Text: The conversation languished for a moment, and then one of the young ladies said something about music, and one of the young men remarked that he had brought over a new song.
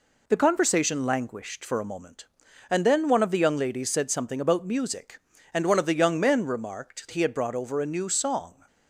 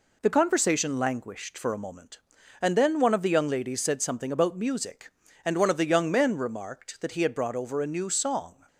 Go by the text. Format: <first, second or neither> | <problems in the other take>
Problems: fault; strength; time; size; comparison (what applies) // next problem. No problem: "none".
second | skips "that"; at 7.0 s